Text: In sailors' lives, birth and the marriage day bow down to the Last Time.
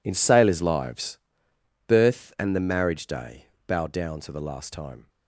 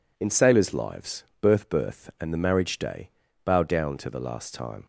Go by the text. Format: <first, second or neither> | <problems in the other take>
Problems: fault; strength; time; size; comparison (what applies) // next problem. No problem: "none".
first | says "birth" twice; at 1.6 s // pauses between "day" and "bow"; slight; at 3.0 s; 0.34 s long; slight in the first